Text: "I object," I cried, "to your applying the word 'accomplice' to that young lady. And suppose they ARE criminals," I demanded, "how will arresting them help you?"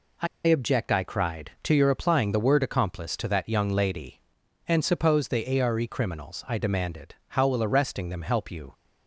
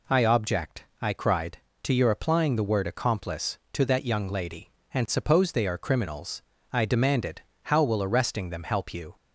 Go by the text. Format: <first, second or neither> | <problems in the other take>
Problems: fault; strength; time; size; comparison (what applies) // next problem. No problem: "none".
second | pauses between "I" and "object"; slight; at 0.2 s; 0.19 s long